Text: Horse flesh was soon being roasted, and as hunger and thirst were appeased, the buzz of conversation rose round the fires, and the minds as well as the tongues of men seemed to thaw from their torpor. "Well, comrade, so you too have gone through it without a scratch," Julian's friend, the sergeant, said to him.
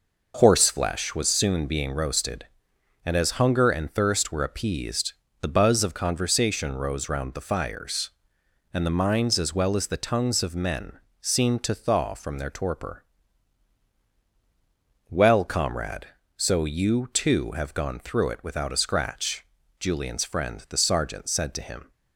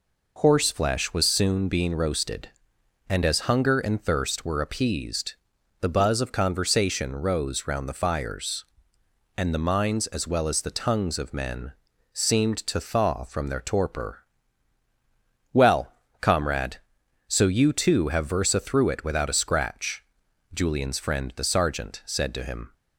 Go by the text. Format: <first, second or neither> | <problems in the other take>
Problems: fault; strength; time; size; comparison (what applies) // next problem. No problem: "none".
first | pauses between "men" and "seemed"; at 11.7 s; 0.42 s long; slight in the first // says "versa" for "gone"; at 18.2 s